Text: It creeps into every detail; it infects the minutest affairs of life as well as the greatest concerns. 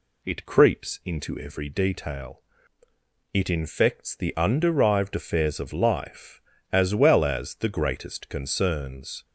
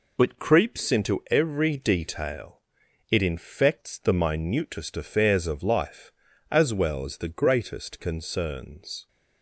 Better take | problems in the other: second | says "underived" for "minutest"; at 4.3 s

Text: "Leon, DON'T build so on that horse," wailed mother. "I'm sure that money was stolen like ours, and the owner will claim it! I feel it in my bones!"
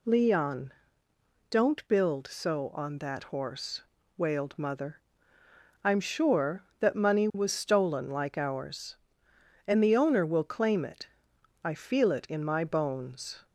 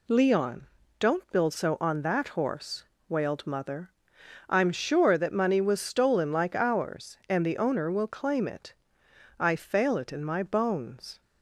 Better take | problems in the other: first | says "fail" for "feel"; at 9.5 s

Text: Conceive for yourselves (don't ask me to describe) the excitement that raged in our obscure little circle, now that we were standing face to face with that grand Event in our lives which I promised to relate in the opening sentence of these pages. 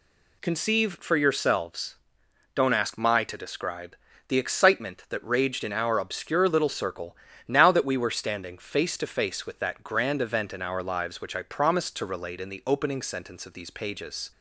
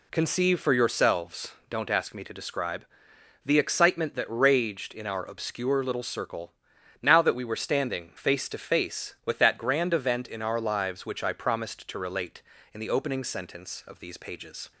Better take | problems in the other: second | says "my" for "me"; at 2.9 s

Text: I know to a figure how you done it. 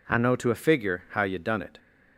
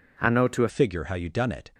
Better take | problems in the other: first | changes voice at "figure"; from 0.6 s on; 1.1 s long

